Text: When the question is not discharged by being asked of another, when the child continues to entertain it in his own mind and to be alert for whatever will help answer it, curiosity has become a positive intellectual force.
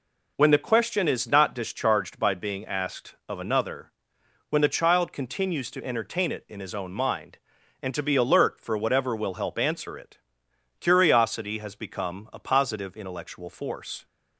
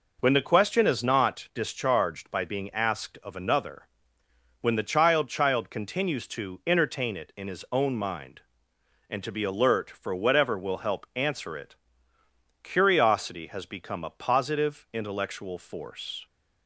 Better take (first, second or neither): first